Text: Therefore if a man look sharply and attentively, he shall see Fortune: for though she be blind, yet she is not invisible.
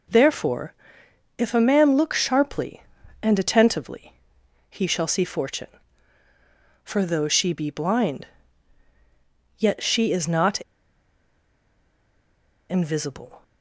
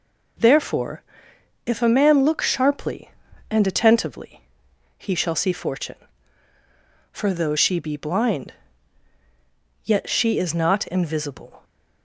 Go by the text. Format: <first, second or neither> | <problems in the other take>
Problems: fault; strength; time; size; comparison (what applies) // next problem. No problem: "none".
second | pauses between "Therefore" and "if"; noticeable; at 0.7 s; 0.64 s long; noticeable in the second // pauses between "not" and "invisible"; strong; at 10.5 s; 2.1 s long